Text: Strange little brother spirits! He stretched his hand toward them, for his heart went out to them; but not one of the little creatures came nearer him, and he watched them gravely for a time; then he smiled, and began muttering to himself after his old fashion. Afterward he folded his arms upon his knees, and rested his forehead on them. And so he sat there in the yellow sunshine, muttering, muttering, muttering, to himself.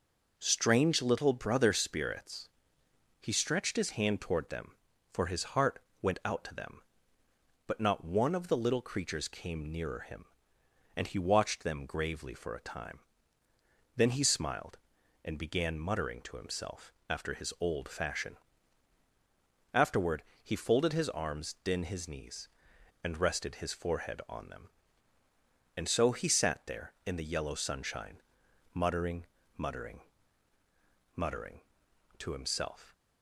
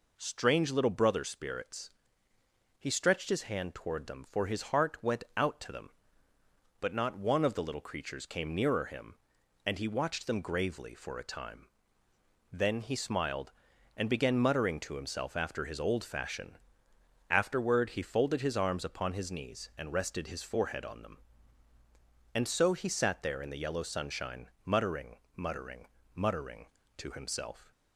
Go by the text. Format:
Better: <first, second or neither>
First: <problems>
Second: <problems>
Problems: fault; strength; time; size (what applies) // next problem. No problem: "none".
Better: second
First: pauses between "heart" and "went"; slight; at 5.7 s; 0.24 s long // pauses between "himself" and "after"; slight; at 16.9 s; 0.16 s long // pauses between "Afterward" and "he"; slight; at 20.2 s; 0.22 s long // says "din" for "upon"; at 21.6 s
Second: none